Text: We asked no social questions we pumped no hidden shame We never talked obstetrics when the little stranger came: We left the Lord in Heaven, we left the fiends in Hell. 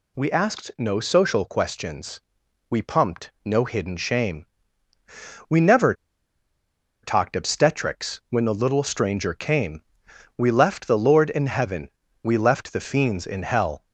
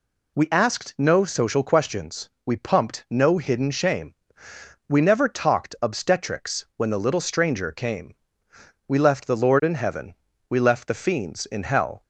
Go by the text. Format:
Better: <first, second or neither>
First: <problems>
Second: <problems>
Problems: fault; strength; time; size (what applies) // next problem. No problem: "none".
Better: second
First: pauses between "questions" and "we"; noticeable; at 2.2 s; 0.48 s long // pauses between "shame" and "We"; at 4.4 s; 1.0 s long // pauses between "never" and "talked"; at 5.9 s; 1.0 s long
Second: pauses between "questions" and "we"; slight; at 2.2 s; 0.16 s long // pauses between "shame" and "We"; noticeable; at 4.1 s; 0.72 s long